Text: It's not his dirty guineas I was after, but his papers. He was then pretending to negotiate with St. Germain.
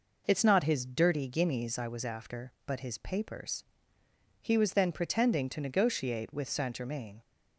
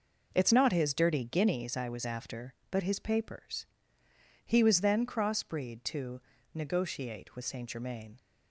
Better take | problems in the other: first | says "crossbreed" for "pretending"; at 5.0 s // pauses between "to" and "negotiate"; slight; at 6.1 s; 0.34 s long

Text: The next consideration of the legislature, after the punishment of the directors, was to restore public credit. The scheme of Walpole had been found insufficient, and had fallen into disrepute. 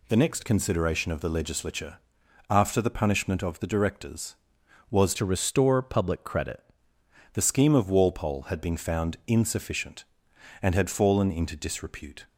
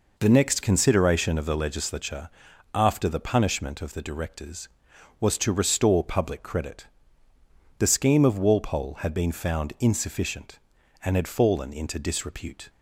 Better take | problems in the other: second | changes voice from "to" to "credit"; from 5.1 to 6.6 s; 1.5 s long

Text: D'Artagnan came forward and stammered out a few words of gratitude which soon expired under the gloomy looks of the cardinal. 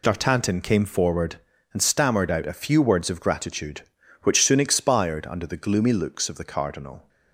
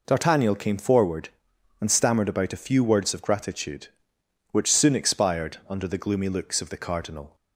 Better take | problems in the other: first | says "about" for "out"; at 2.2 s

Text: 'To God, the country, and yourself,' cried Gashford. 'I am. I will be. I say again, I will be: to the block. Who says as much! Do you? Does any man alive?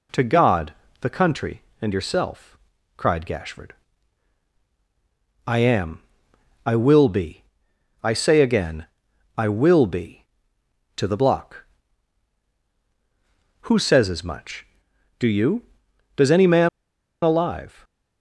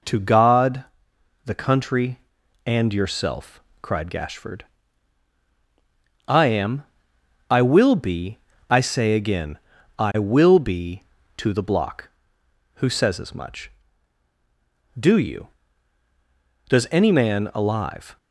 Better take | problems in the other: second | pauses between "man" and "alive"; noticeable; at 16.6 s; 0.55 s long

